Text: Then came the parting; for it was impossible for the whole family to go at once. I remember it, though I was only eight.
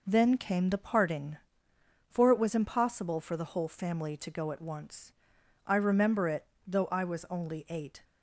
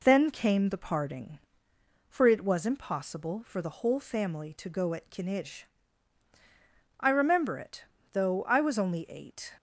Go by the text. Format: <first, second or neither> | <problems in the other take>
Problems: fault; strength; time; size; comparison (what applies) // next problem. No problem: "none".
first | says "kinij" for "once"; at 5.1 s